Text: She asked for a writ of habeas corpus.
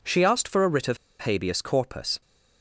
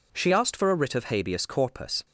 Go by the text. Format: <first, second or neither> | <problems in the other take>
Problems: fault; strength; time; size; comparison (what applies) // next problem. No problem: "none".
second | pauses between "of" and "habeas"; slight; at 0.9 s; 0.23 s long